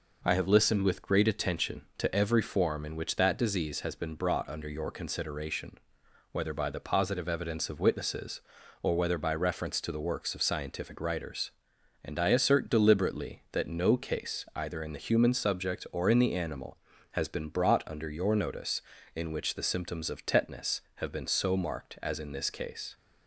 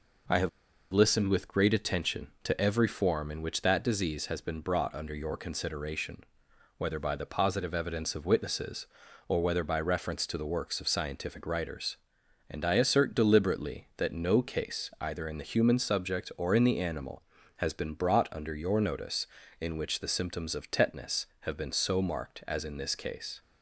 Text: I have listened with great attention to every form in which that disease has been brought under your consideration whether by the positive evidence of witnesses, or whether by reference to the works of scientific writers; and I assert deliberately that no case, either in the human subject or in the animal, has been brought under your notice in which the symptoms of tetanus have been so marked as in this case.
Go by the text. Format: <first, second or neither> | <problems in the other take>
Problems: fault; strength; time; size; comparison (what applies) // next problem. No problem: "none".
first | pauses between "have" and "listened"; at 0.4 s; 0.42 s long // pauses between "consideration" and "whether"; noticeable; at 6.2 s; 0.52 s long; noticeable in the first